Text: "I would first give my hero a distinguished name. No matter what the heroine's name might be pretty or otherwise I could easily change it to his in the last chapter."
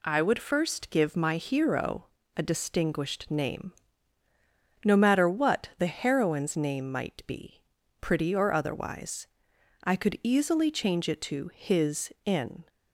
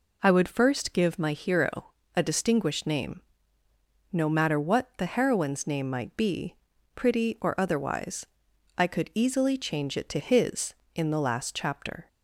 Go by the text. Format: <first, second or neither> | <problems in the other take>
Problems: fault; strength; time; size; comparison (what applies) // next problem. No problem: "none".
second | pauses between "hero" and "a"; slight; at 2.0 s; 0.28 s long; slight in the second // pauses between "be" and "pretty"; at 7.6 s; 0.38 s long; also in the second // pauses between "otherwise" and "I"; noticeable; at 9.2 s; 0.56 s long; noticeable in the second // stops before "the last chapter"; at 12.6 s